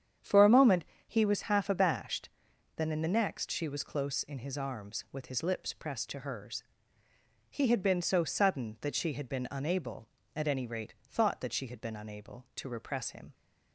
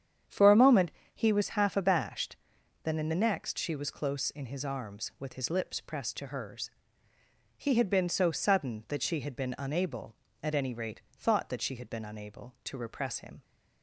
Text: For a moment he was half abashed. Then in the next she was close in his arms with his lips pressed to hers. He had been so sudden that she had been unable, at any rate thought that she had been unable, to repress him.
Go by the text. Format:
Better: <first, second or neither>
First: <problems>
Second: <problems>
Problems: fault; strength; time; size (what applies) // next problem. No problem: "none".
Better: neither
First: starts louder than the rest; strong; until 1.4 s; 8.5 dB // pauses between "moment" and "he"; slight; at 0.8 s; 0.25 s long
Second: starts louder than the rest; strong; until 1.5 s; 8.5 dB // pauses between "moment" and "he"; slight; at 0.8 s; 0.24 s long